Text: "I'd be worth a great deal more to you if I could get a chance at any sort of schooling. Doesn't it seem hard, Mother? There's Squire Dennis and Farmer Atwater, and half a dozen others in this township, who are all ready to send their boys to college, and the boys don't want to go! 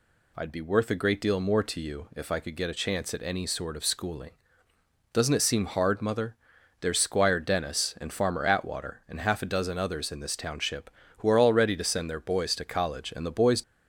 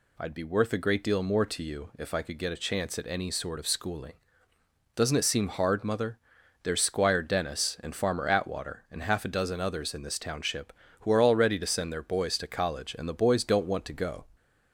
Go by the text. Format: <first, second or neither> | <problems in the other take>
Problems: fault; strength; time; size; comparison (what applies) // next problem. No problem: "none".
second | stops before "don't want to go"; at 13.6 s